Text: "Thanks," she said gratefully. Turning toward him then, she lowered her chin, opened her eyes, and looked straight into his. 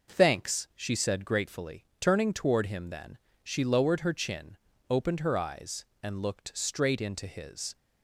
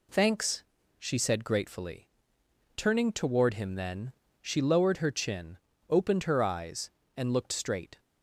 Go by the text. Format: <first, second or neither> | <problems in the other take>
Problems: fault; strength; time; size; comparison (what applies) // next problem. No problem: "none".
first | stops before "into his"; at 7.9 s